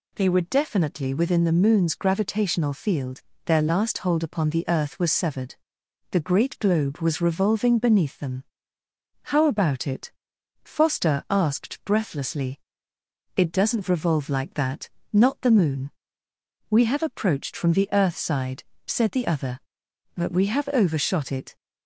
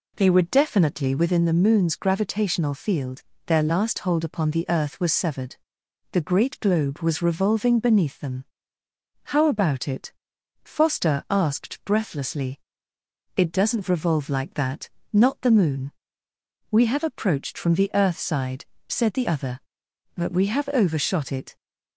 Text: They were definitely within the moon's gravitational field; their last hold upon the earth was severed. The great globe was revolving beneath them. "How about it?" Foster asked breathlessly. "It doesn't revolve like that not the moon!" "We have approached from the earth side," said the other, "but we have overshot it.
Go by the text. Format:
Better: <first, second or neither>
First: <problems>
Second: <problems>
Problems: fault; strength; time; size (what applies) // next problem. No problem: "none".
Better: first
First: pauses between "that" and "not"; slight; at 14.8 s; 0.24 s long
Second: starts louder than the rest; slight; until 1.4 s; 3 dB // pauses between "that" and "not"; slight; at 14.8 s; 0.24 s long